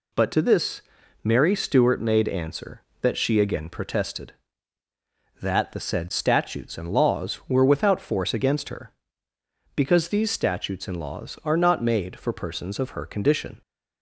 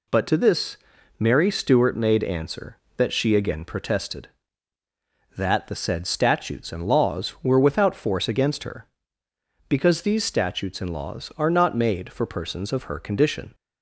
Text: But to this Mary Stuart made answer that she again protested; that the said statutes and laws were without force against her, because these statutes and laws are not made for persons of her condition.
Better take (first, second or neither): neither